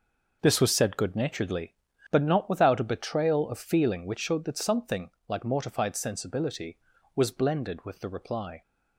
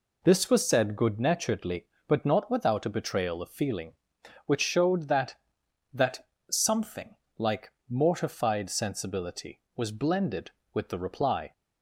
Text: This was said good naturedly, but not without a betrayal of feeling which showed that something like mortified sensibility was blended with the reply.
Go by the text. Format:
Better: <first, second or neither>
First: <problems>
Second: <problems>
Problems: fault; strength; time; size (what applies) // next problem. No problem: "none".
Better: first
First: pauses between "something" and "like"; slight; at 5.0 s; 0.18 s long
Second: says "that" twice; at 5.9 s // pauses between "something" and "like"; slight; at 7.1 s; 0.22 s long // pauses between "like" and "mortified"; slight; at 7.7 s; 0.16 s long